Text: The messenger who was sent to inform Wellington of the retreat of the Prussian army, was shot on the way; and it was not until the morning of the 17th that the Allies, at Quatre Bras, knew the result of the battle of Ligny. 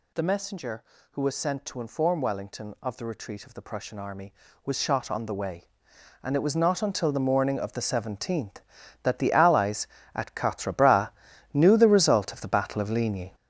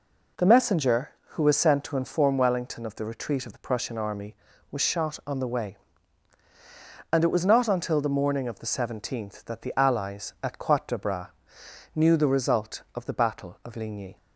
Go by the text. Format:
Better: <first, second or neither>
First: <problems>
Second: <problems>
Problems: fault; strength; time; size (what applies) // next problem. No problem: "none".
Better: second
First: gets louder; strong; throughout; 8 dB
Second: none